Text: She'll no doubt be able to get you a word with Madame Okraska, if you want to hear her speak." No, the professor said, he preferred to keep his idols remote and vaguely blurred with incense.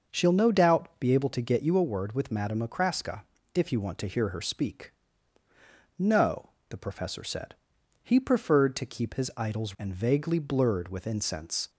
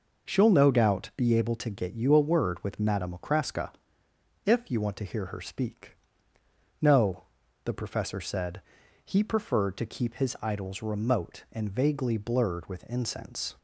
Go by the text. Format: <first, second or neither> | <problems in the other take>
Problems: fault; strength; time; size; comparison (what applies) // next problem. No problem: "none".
second | starts louder than the rest; noticeable; until 1.2 s; 6 dB // skips "remote"; at 9.7 s